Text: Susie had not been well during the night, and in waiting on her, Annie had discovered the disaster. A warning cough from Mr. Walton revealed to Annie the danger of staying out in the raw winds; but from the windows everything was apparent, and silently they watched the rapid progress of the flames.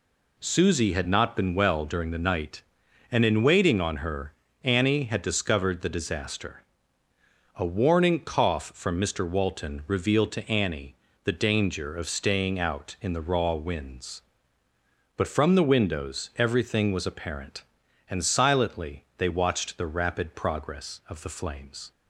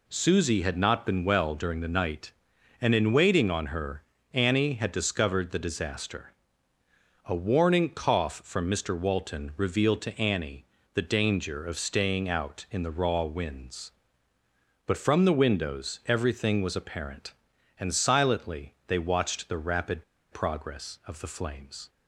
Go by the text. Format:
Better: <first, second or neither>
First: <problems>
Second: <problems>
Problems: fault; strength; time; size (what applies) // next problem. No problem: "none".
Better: first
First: pauses between "Annie" and "the"; slight; at 10.9 s; 0.26 s long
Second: pauses between "Annie" and "the"; slight; at 10.6 s; 0.26 s long // pauses between "rapid" and "progress"; slight; at 20.0 s; 0.28 s long